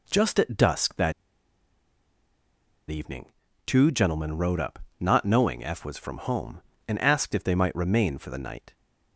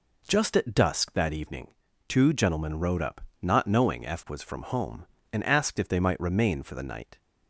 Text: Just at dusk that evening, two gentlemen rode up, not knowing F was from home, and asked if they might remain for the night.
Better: second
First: pauses between "that" and "evening"; strong; at 1.1 s; 1.7 s long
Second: none

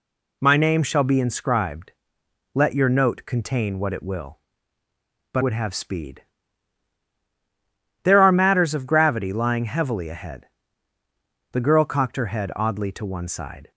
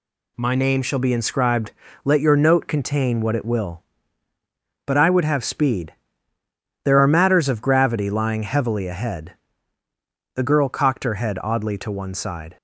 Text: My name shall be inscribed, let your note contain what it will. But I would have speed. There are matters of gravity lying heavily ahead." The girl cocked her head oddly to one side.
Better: second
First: skips "I"; at 5.4 s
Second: none

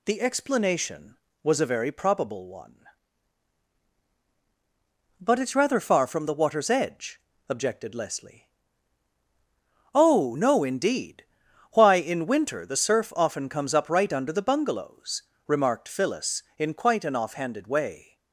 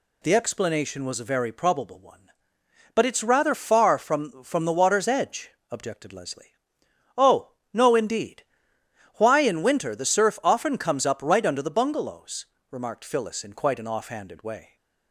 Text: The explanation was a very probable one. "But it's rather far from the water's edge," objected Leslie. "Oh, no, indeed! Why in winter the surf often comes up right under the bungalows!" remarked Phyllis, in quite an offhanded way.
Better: first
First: none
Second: says "from" twice; at 4.4 s

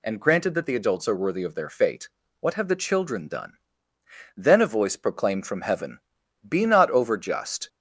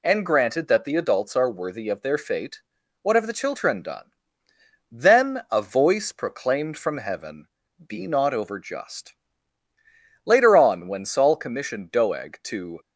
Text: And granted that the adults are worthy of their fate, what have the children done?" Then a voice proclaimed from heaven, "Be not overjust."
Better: first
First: none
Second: goes on to say "Later on when Saul commissioned Doeg to"; strong; from 10.2 s on; 2.5 s long

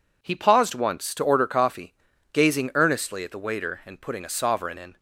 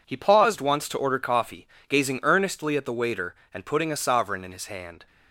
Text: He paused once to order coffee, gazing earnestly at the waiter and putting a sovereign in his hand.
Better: second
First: stops before "his hand"; at 4.9 s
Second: none

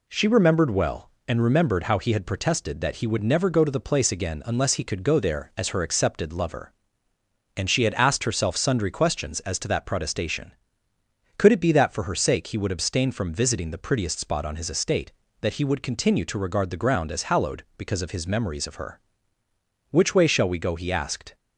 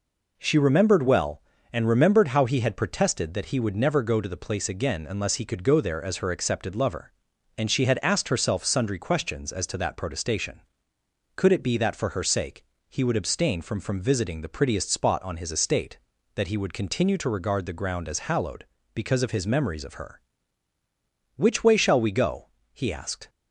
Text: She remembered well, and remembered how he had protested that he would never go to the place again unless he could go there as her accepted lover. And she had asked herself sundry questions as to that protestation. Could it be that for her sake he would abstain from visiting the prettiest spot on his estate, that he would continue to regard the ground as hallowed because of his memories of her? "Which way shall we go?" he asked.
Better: first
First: none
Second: pauses between "sake" and "he"; slight; at 12.6 s; 0.24 s long // says "from" twice; at 13.7 s

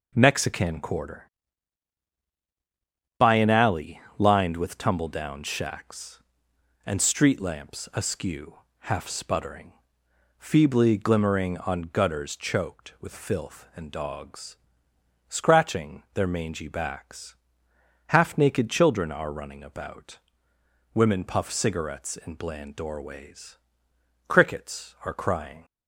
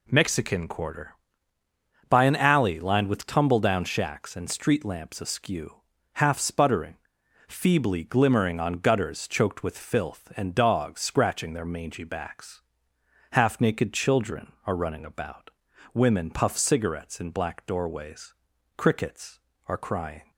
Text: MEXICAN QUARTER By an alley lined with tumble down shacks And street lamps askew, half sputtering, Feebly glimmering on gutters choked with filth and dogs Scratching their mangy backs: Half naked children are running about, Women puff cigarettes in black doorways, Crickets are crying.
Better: second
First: pauses between "alley" and "lined"; slight; at 3.9 s; 0.20 s long // pauses between "dogs" and "Scratching"; noticeable; at 14.5 s; 0.74 s long // says "bland" for "black"; at 22.3 s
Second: none

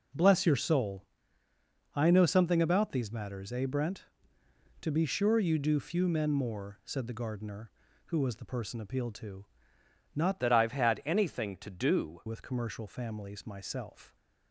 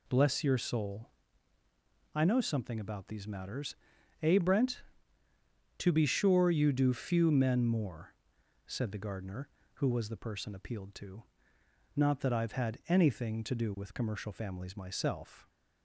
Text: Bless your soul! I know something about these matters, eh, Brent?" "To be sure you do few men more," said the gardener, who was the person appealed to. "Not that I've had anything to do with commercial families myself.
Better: second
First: changes voice from "that" to "do"; from 10.4 to 12.2 s; 1.8 s long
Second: none

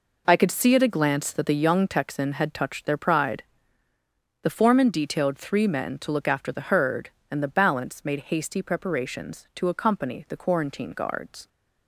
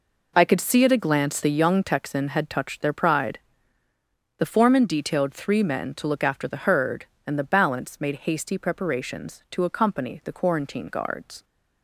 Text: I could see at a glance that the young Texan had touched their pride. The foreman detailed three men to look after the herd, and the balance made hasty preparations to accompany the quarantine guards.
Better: first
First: none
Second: skips "that"; at 1.4 s

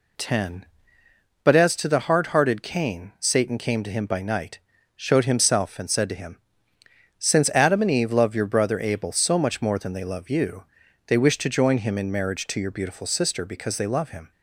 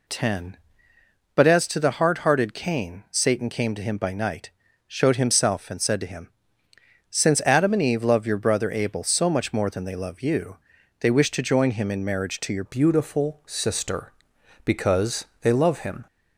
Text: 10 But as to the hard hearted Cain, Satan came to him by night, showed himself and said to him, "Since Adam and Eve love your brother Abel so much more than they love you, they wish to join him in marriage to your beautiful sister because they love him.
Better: first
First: none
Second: changes voice at "beautiful"; from 12.6 s on; 3.4 s long // pauses between "because" and "they"; slight; at 15.2 s; 0.18 s long

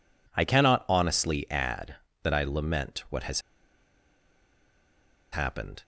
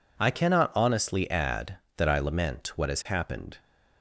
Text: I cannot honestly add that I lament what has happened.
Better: second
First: pauses between "has" and "happened"; strong; at 3.4 s; 1.9 s long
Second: none

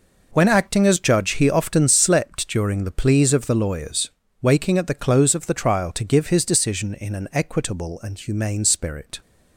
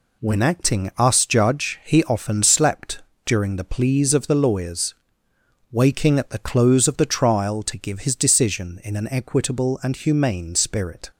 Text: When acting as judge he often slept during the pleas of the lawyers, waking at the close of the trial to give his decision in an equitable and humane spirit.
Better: first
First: none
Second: says "us" for "as"; at 0.9 s // pauses between "slept" and "during"; slight; at 3.0 s; 0.22 s long

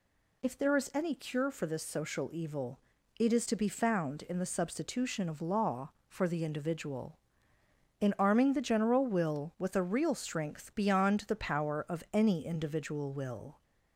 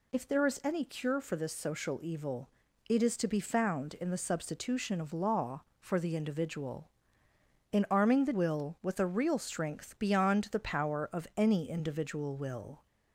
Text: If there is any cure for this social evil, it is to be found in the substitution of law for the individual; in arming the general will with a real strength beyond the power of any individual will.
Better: first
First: none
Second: skips "general"; at 8.3 s

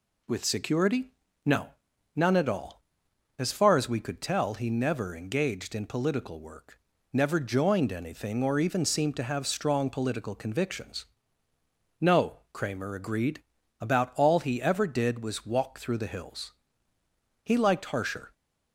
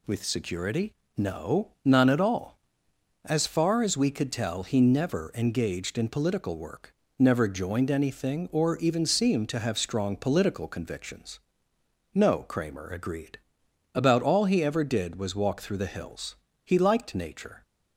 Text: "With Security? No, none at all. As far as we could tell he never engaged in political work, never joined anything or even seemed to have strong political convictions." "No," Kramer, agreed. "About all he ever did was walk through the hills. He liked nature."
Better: second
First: says "harsher" for "nature"; at 17.8 s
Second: none

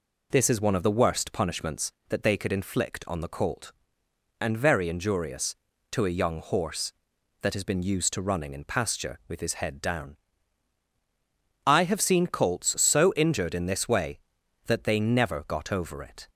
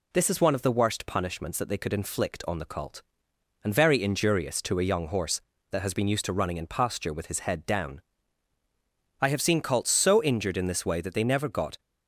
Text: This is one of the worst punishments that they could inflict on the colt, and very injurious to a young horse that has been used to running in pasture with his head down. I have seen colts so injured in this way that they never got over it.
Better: first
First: none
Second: stops before "over it"; at 11.7 s

